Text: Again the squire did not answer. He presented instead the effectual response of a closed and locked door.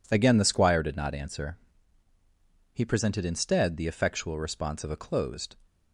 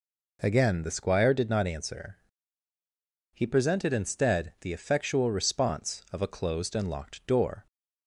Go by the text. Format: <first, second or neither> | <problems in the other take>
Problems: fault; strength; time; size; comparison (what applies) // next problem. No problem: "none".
second | stops before "and locked door"; at 5.6 s